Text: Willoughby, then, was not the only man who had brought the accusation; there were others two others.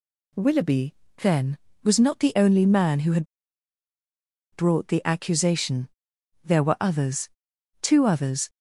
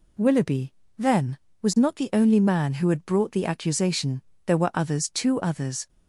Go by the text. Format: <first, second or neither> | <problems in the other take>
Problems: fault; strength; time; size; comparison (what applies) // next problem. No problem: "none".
second | pauses between "had" and "brought"; strong; at 3.2 s; 1.2 s long // pauses between "others" and "two"; noticeable; at 7.2 s; 0.54 s long